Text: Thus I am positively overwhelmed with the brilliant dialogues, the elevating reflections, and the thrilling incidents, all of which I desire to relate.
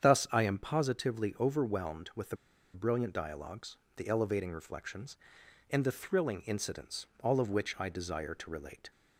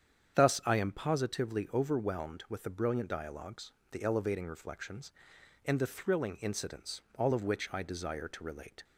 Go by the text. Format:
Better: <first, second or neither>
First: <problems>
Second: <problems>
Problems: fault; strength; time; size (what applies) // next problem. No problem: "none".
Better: second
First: starts louder than the rest; strong; until 1.0 s; 8 dB // pauses between "the" and "brilliant"; at 2.3 s; 0.37 s long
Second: starts louder than the rest; strong; until 1.3 s; 8 dB